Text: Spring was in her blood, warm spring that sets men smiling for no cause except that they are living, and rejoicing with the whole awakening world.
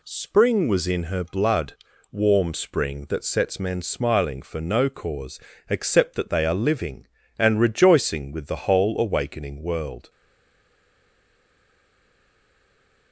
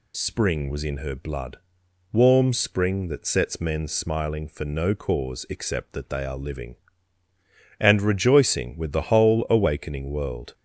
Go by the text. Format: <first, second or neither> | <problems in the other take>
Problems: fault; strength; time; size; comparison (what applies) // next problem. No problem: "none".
second | pauses between "cause" and "except"; slight; at 5.3 s; 0.30 s long // stays silent after the last word; strong; from 10.0 s on; 3.1 s long